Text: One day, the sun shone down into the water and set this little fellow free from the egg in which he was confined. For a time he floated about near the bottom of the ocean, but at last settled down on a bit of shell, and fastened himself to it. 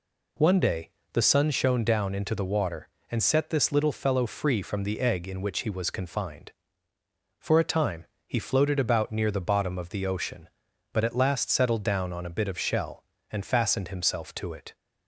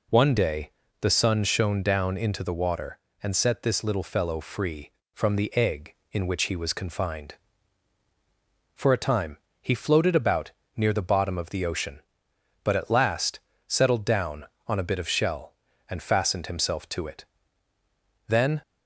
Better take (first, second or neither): first